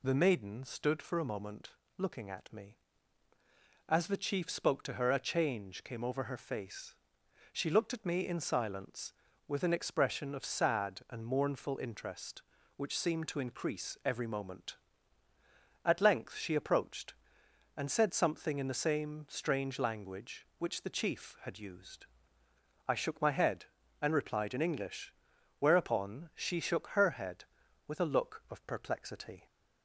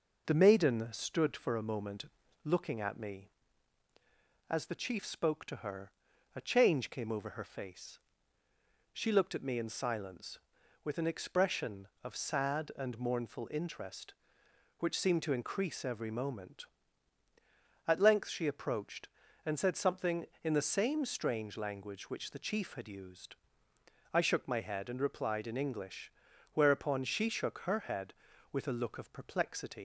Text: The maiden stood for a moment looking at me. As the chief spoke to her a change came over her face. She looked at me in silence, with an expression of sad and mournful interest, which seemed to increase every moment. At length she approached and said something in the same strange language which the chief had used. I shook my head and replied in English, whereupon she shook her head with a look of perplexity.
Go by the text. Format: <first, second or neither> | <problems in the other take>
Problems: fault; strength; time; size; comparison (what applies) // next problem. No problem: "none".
first | pauses between "moment" and "looking"; at 2.0 s; 0.38 s long; slight in the first // pauses between "her" and "a"; at 5.9 s; 0.44 s long // leaves "perplexity" unfinished; at 29.7 s; 90 ms